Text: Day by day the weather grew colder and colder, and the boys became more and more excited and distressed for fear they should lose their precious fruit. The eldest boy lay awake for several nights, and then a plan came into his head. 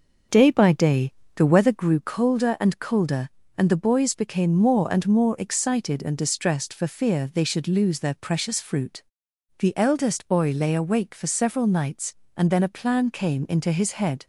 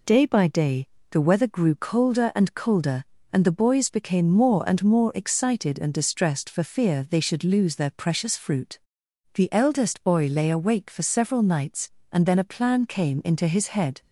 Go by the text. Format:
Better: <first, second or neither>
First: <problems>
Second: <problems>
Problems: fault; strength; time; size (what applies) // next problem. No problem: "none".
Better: second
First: starts louder than the rest; until 1.9 s; 6.5 dB // pauses between "day" and "the"; slight; at 1.1 s; 0.26 s long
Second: pauses between "day" and "the"; slight; at 0.8 s; 0.26 s long